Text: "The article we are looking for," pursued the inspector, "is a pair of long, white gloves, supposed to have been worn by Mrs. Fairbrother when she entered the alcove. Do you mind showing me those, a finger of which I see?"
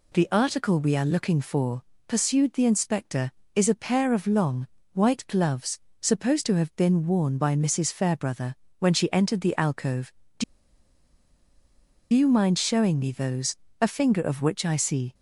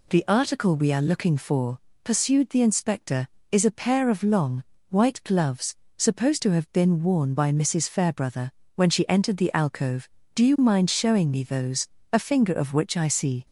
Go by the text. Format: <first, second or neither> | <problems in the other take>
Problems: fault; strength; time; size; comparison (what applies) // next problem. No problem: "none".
second | pauses between "Fairbrother" and "when"; slight; at 8.5 s; 0.24 s long; slight in the second // pauses between "Do" and "you"; strong; at 10.4 s; 1.6 s long